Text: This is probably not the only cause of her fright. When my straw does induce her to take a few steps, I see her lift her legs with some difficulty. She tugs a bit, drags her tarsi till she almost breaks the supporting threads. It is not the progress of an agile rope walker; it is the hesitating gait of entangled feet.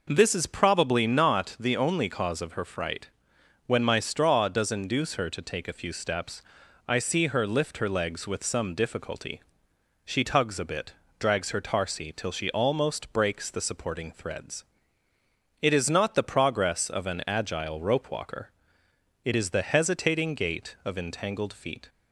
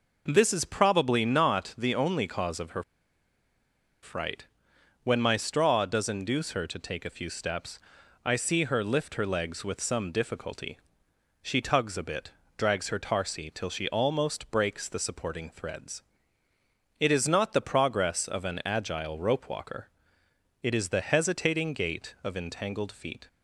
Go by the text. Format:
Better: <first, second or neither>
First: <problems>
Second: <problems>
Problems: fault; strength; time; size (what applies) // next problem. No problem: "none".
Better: first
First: none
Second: pauses between "her" and "fright"; at 2.8 s; 1.2 s long